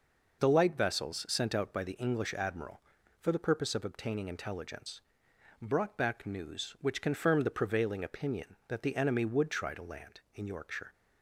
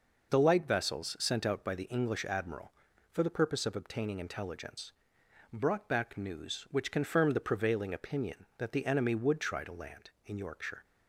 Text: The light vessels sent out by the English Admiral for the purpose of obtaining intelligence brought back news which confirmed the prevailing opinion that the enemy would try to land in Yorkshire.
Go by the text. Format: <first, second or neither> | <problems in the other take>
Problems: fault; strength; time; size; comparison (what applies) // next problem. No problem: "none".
neither | pauses between "intelligence" and "brought"; noticeable; the same in both